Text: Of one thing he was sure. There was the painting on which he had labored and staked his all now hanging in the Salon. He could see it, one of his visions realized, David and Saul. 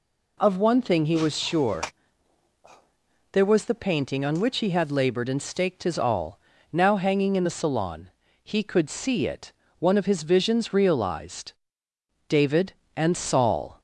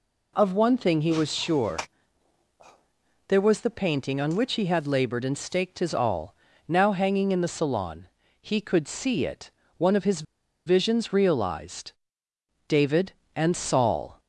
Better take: first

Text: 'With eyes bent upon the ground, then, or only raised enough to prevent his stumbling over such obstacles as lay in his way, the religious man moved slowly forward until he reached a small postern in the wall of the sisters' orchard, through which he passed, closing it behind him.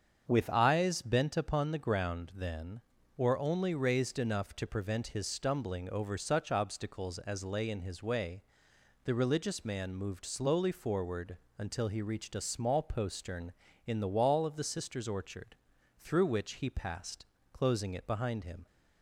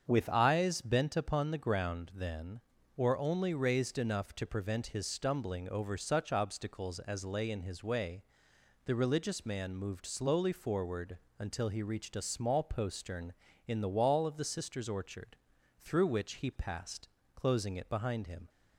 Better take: neither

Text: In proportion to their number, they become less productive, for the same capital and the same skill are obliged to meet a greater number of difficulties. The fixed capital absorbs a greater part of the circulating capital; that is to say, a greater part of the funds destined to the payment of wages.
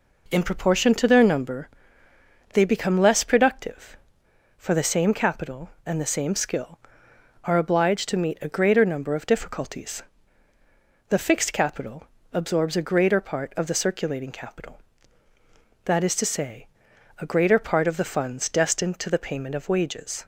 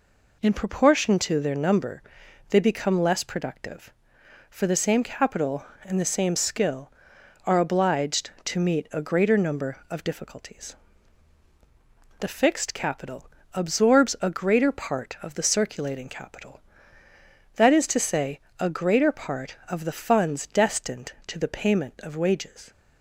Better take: neither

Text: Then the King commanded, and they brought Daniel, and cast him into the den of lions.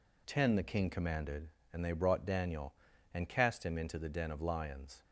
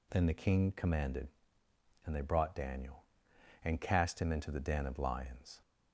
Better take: second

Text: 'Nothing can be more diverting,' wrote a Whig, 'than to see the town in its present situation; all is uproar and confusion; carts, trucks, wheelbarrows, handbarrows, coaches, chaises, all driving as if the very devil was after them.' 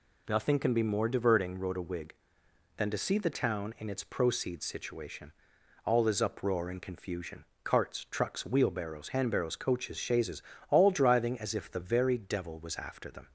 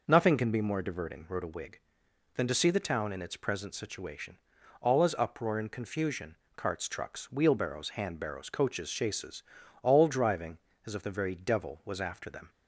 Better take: second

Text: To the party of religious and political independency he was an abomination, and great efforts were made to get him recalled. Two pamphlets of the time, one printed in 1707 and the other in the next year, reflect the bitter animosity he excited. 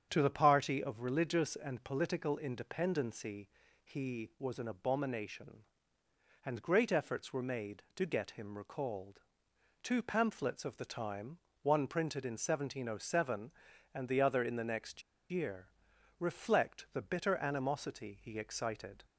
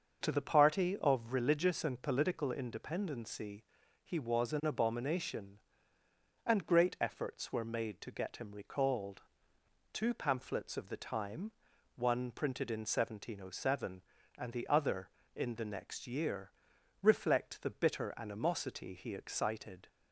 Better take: second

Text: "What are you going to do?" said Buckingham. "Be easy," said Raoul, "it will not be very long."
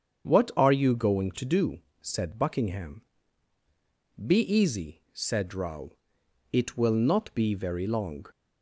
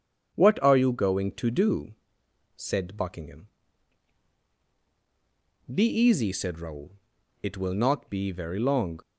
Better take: neither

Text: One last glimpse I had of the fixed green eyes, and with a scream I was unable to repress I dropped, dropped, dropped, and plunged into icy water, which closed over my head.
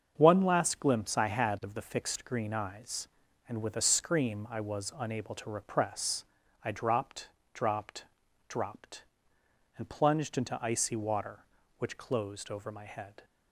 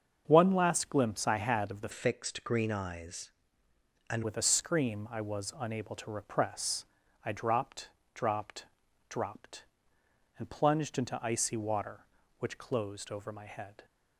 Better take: first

